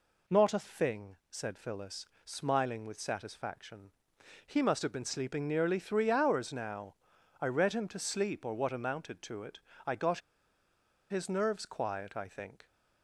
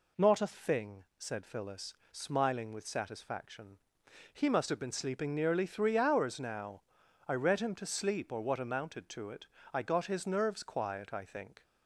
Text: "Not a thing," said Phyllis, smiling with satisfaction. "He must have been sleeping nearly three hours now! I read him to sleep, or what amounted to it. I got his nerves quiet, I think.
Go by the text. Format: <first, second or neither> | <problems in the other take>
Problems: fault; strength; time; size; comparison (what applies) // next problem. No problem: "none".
second | pauses between "got" and "his"; noticeable; at 10.1 s; 0.91 s long